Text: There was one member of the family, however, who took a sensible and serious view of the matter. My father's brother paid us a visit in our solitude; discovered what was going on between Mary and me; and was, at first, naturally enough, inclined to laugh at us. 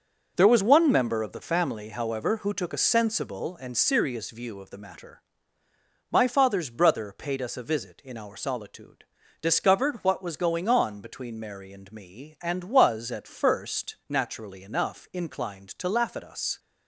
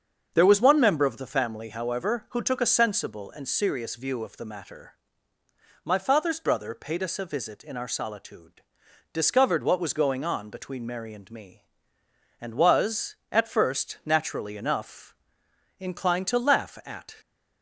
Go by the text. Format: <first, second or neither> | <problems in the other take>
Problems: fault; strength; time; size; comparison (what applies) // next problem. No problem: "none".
first | starts louder than the rest; until 1.3 s; 7 dB; also in the first // stops before "us"; at 17.2 s